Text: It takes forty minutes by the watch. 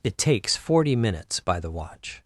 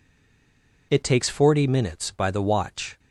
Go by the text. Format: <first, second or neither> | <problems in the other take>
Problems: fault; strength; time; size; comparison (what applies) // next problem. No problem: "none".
first | stays silent before the first word; slight; until 0.9 s; 0.9 s long